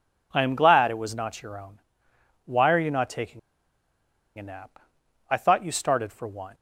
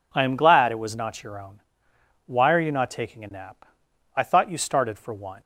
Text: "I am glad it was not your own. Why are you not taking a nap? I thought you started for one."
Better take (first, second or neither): second